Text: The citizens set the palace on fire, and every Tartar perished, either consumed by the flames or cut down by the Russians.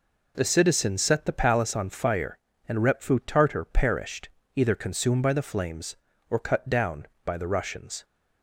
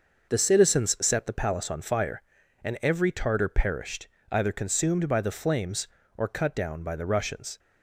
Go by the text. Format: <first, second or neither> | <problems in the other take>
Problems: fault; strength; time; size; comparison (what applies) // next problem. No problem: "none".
second | says "repfu" for "every"; at 2.7 s